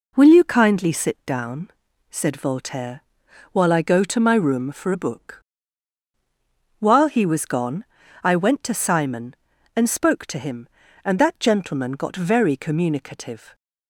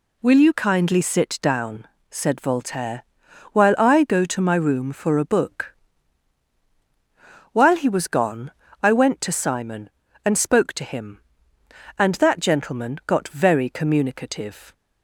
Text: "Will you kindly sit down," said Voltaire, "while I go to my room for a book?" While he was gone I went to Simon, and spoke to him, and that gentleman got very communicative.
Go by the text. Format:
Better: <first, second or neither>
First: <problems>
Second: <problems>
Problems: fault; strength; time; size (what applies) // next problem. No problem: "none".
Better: neither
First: pauses between "gone" and "I"; slight; at 7.8 s; 0.36 s long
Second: pauses between "gone" and "I"; slight; at 8.4 s; 0.32 s long